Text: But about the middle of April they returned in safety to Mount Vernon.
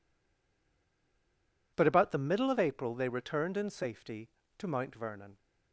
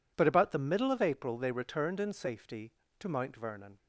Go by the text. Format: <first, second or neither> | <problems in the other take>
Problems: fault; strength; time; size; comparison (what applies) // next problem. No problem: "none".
second | stays silent before the first word; noticeable; until 1.7 s; 1.7 s long